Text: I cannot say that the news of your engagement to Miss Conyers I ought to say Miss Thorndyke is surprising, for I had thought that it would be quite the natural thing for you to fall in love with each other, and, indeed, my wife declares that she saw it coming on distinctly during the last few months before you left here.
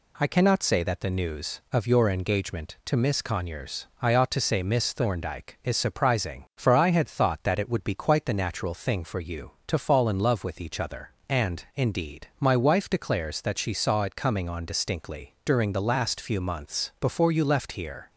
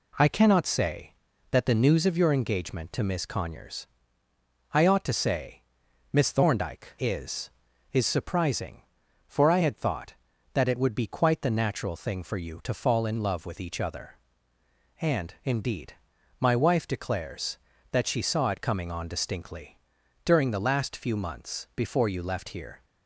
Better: first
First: none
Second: pauses between "Conyers" and "I"; noticeable; at 3.8 s; 0.84 s long // pauses between "say" and "Miss"; noticeable; at 5.6 s; 0.50 s long // says "is" twice; at 7.9 s // pauses between "distinctly" and "during"; at 19.7 s; 0.44 s long

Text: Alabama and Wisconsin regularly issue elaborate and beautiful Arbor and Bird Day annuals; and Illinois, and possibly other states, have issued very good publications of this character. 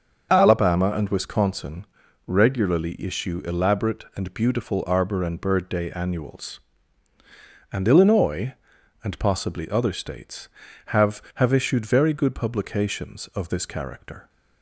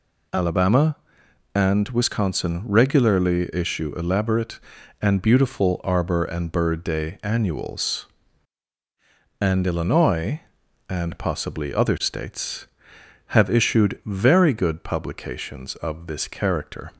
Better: second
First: starts louder than the rest; until 1.3 s; 6.5 dB // pauses between "Wisconsin" and "regularly"; at 1.8 s; 0.42 s long // says "have" twice; at 11.3 s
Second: none

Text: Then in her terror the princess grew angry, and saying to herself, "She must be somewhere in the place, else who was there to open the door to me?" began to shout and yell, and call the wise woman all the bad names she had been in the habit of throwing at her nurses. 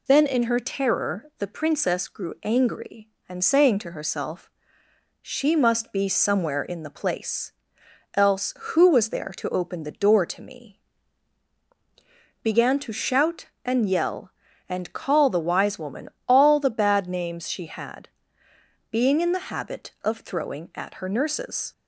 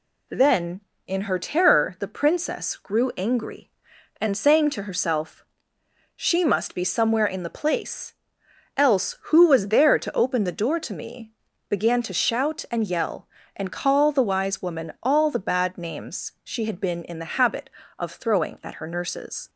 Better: second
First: pauses between "woman" and "all"; slight; at 16.0 s; 0.20 s long // says "being" for "been"; at 18.8 s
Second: none

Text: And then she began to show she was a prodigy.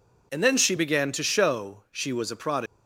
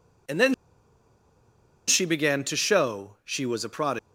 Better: first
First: none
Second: pauses between "then" and "she"; strong; at 0.5 s; 1.3 s long

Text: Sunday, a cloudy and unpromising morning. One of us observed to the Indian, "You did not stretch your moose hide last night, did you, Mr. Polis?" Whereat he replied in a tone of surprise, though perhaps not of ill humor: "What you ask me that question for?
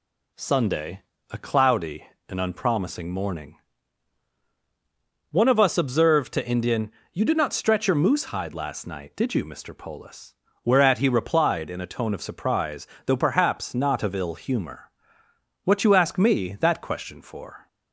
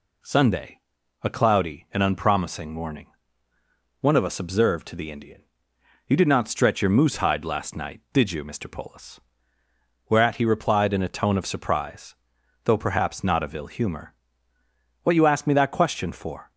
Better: second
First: skips "the"; at 6.4 s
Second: none

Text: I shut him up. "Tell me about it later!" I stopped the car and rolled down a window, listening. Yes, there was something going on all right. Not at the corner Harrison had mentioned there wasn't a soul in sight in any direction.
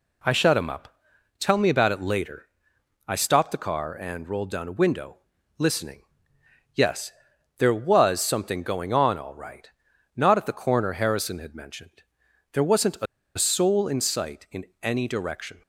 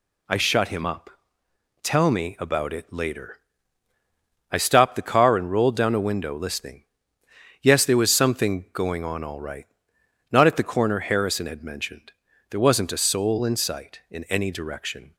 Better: second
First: pauses between "mentioned" and "there"; noticeable; at 12.0 s; 0.50 s long // pauses between "a" and "soul"; slight; at 13.0 s; 0.31 s long // pauses between "in" and "any"; slight; at 14.6 s; 0.16 s long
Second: pauses between "mentioned" and "there"; at 12.1 s; 0.38 s long

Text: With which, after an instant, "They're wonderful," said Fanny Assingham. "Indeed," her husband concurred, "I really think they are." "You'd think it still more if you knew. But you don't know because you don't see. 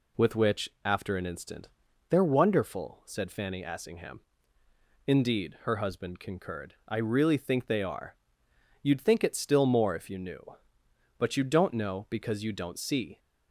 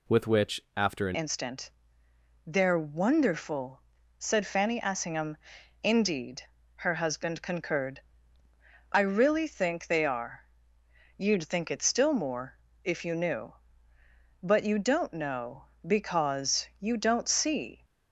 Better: first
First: none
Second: changes voice at "instant"; from 1.1 s on; 16.7 s long // pauses between "more" and "if"; slight; at 12.5 s; 0.28 s long

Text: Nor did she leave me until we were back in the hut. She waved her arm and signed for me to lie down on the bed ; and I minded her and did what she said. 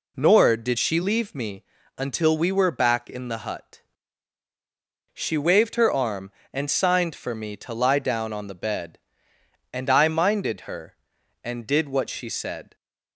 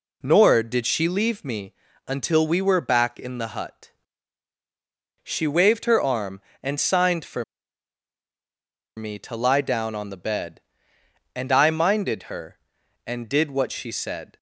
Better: first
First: pauses between "me" and "until"; slight; at 1.6 s; 0.34 s long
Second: pauses between "me" and "until"; slight; at 1.7 s; 0.34 s long // pauses between "for" and "me"; strong; at 7.4 s; 1.5 s long

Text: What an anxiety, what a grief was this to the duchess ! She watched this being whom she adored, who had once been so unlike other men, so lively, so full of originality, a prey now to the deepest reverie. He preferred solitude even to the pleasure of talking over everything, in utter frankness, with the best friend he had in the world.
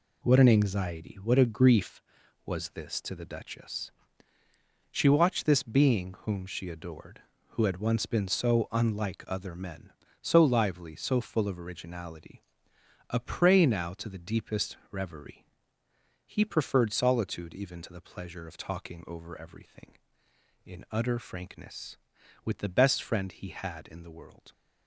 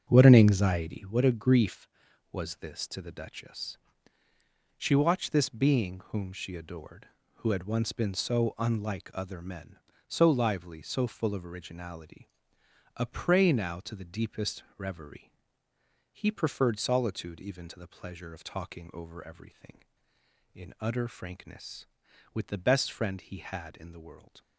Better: first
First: pauses between "deepest" and "reverie"; slight; at 14.7 s; 0.16 s long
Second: starts louder than the rest; until 1.1 s; 7 dB // pauses between "deepest" and "reverie"; slight; at 14.6 s; 0.16 s long

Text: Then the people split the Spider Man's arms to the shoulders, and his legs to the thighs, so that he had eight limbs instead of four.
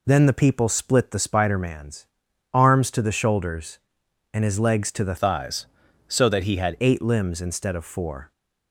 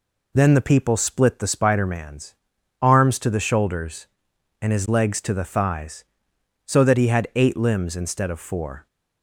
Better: second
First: pauses between "Man's" and "arms"; noticeable; at 2.0 s; 0.48 s long // changes voice from "thighs" to "had"; from 5.1 to 6.7 s; 1.6 s long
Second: pauses between "Man's" and "arms"; noticeable; at 2.3 s; 0.48 s long

